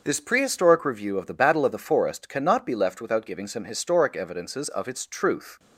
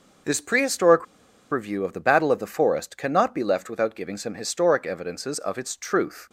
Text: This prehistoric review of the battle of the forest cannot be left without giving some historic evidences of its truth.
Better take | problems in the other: first | pauses between "prehistoric" and "review"; noticeable; at 1.0 s; 0.46 s long

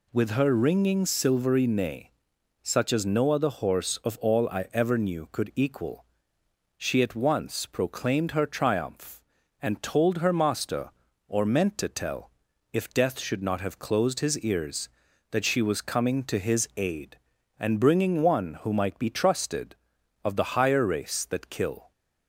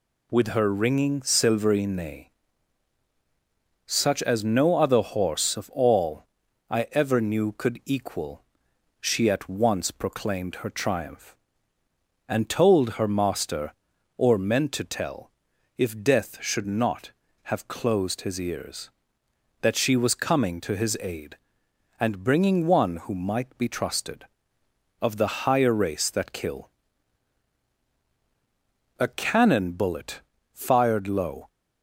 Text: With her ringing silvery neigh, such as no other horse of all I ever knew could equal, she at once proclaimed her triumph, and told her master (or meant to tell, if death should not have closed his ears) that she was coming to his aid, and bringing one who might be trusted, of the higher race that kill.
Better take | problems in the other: first | pauses between "all" and "I"; at 6.2 s; 0.44 s long // goes on to say "A cannon bullet fired low"; strong; from 28.9 s on; 2.4 s long

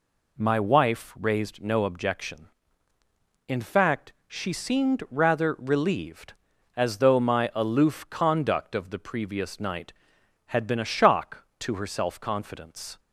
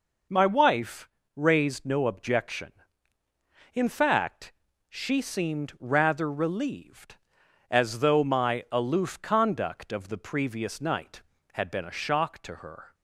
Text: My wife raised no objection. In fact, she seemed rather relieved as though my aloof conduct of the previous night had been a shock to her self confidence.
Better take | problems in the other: first | pauses between "wife" and "raised"; slight; at 1.0 s; 0.28 s long // stops before "self confidence"; at 12.9 s

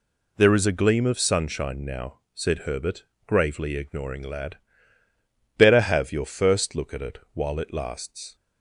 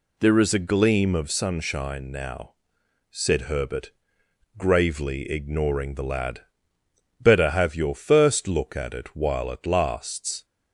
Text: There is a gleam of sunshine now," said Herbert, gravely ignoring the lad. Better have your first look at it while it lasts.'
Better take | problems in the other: second | skips "the"; at 4.2 s // pauses between "it" and "while"; slight; at 7.1 s; 0.16 s long

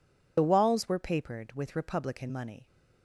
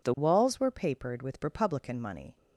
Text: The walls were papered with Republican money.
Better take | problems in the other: second | loses the start of "The"; at 0.3 s; 50 ms

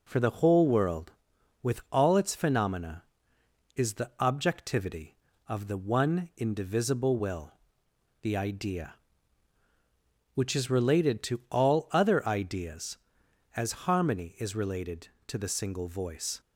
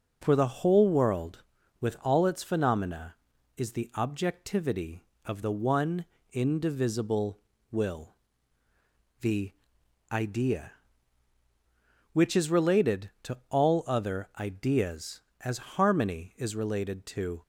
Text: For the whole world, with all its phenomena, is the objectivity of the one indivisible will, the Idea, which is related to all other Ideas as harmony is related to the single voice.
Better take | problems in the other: first | pauses between "one" and "indivisible"; slight; at 6.0 s; 0.28 s long // pauses between "the" and "Idea"; noticeable; at 9.5 s; 0.60 s long // stops before "the single voice"; at 17.4 s

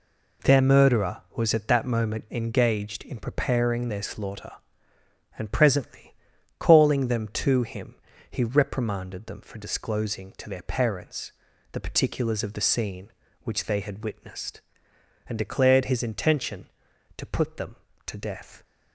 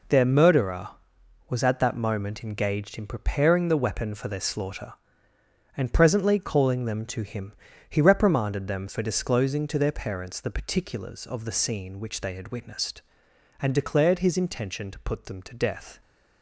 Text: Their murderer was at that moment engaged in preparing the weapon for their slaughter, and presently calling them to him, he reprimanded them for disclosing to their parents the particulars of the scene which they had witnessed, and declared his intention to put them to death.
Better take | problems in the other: second | skips "the weapon for"; at 3.8 s // pauses between "presently" and "calling"; at 6.1 s; 0.44 s long // pauses between "parents" and "the"; at 11.3 s; 0.40 s long

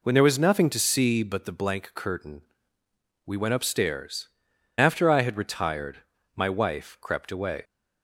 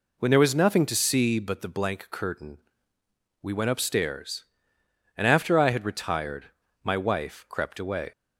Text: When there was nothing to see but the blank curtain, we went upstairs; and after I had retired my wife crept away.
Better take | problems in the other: second | skips "and"; at 4.5 s // pauses between "retired" and "my"; at 5.9 s; 0.38 s long; also in the second

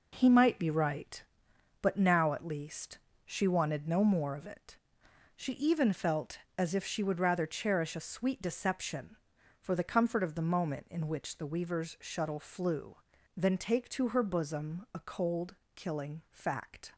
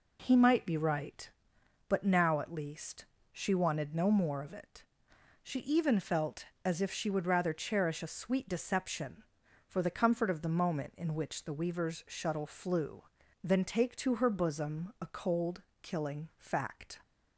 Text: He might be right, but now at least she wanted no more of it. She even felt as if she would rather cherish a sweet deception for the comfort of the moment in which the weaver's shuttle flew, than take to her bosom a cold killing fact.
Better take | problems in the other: second | gets quieter; strong; throughout; 7.5 dB // pauses between "least" and "she"; slight; at 2.9 s; 0.26 s long; slight in the second // pauses between "cold" and "killing"; slight; at 15.5 s; 0.18 s long; slight in the second

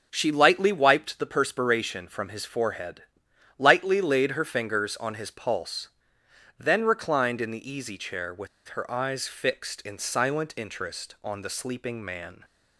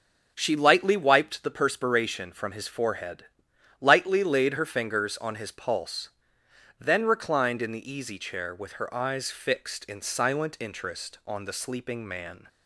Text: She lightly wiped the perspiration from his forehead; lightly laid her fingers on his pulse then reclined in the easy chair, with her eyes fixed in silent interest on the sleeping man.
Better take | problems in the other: second | pauses between "pulse" and "then"; noticeable; at 5.8 s; 0.72 s long; noticeable in the second // pauses between "with" and "her"; slight; at 8.4 s; 0.20 s long

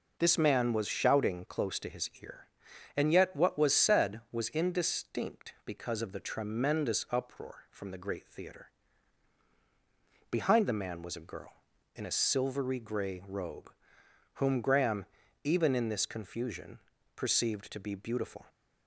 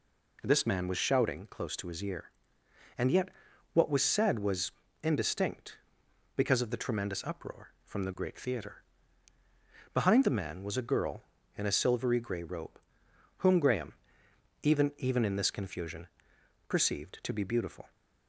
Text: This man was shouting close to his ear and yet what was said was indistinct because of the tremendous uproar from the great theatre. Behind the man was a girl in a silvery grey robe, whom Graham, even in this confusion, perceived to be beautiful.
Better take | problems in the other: first | pauses between "yet" and "what"; at 3.2 s; 0.44 s long // pauses between "was" and "indistinct"; slight; at 4.7 s; 0.30 s long // says "even" twice; at 14.9 s

